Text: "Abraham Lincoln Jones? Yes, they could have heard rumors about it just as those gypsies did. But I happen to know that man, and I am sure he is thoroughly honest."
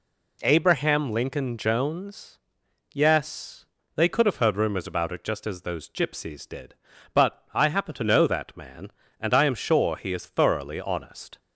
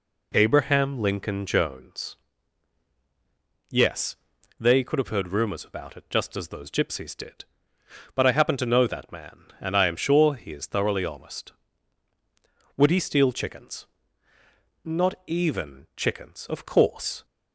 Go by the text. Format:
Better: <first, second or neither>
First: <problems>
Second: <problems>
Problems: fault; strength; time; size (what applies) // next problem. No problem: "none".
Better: first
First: none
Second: goes on to say "Would he steal chickens Not even chickens Of course"; strong; from 12.7 s on; 4.4 s long